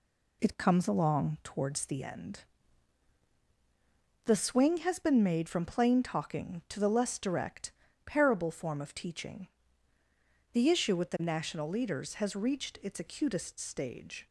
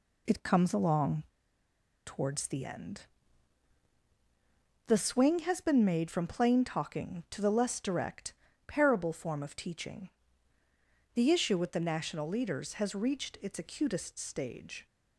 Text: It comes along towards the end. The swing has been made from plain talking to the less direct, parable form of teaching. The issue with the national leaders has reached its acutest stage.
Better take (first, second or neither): first